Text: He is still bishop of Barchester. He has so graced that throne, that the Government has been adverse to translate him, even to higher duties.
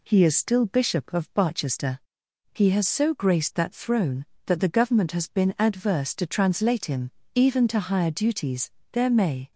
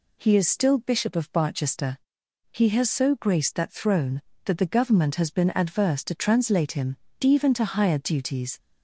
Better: second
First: goes on to say "There may"; from 8.9 s on; 0.60 s long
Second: none

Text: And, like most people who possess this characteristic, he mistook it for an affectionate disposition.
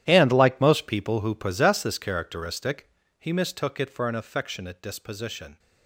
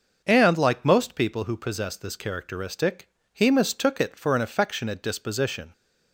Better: second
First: gets quieter; strong; throughout; 17 dB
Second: none

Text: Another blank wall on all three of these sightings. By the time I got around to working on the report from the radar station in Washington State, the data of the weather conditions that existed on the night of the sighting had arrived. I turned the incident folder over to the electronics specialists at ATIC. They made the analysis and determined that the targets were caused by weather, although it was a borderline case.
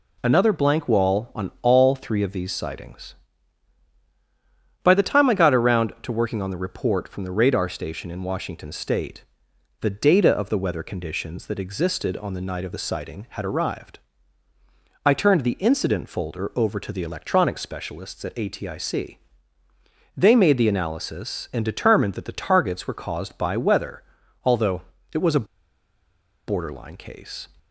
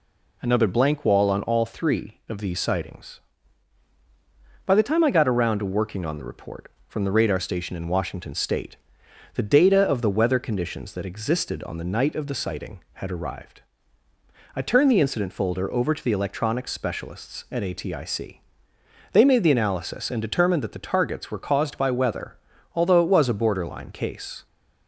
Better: second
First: pauses between "although" and "it"; slight; at 24.8 s; 0.32 s long // pauses between "a" and "borderline"; at 25.4 s; 1.0 s long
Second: none

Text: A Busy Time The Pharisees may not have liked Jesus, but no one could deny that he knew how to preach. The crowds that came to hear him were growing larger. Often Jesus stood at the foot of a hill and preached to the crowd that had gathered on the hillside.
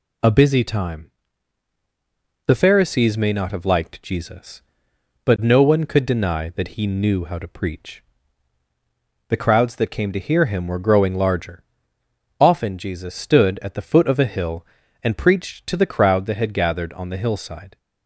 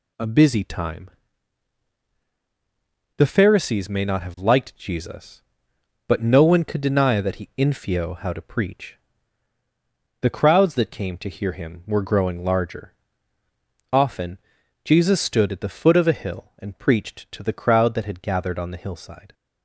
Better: first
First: pauses between "Time" and "The"; strong; at 1.1 s; 1.3 s long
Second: pauses between "Time" and "The"; strong; at 1.1 s; 2.0 s long // says "infio" for "knew"; at 7.5 s // pauses between "Often" and "Jesus"; at 14.3 s; 0.44 s long

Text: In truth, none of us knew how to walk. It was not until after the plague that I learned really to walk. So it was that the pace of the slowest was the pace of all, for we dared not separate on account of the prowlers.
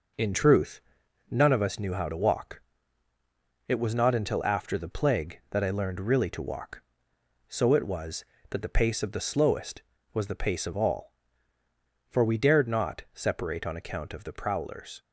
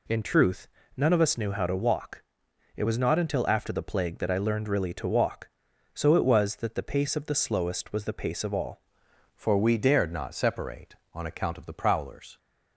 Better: first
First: none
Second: changes voice at "for"; from 9.3 s on; 3.0 s long

